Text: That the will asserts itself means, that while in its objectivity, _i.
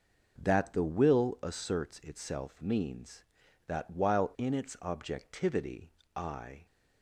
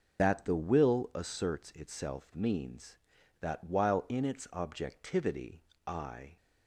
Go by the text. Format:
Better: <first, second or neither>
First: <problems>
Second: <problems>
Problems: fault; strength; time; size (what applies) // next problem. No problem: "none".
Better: first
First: none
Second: loses the start of "That"; at 0.1 s; 125 ms